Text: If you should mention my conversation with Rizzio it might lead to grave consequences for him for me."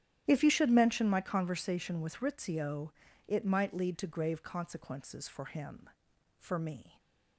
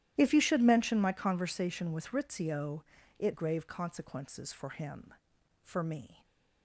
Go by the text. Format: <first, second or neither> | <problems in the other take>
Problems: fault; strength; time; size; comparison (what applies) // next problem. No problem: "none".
first | starts louder than the rest; strong; until 1.1 s; 13 dB; strong in the first // pauses between "Rizzio" and "it"; slight; at 2.8 s; 0.36 s long; slight in the first // skips "might lead to"; at 3.3 s